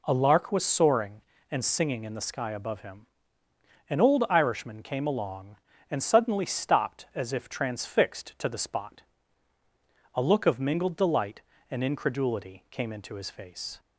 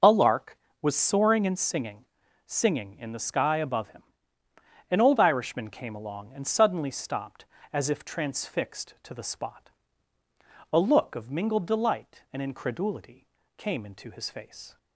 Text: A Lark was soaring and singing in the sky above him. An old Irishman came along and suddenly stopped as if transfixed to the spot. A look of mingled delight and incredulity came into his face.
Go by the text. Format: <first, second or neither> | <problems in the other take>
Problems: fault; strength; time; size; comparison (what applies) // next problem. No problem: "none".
first | says "singing" twice; at 2.4 s // pauses between "incredulity" and "came"; slight; at 13.2 s; 0.32 s long